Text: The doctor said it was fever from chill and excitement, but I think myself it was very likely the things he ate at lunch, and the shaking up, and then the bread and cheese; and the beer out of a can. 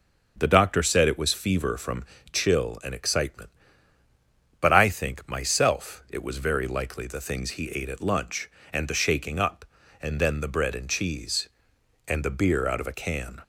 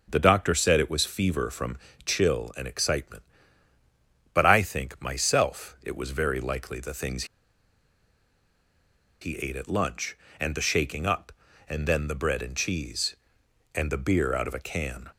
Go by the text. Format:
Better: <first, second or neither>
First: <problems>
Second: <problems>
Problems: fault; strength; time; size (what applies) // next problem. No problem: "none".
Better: first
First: starts louder than the rest; until 1.4 s; 7 dB // pauses between "from" and "chill"; slight; at 2.0 s; 0.28 s long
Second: starts louder than the rest; until 1.1 s; 6.5 dB // pauses between "from" and "chill"; slight; at 1.7 s; 0.28 s long // pauses between "things" and "he"; strong; at 7.2 s; 1.9 s long